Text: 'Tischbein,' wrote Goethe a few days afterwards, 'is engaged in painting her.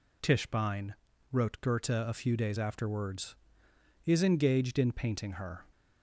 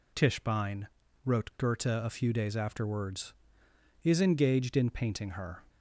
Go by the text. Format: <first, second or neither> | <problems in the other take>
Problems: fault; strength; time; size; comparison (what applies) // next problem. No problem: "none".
neither | none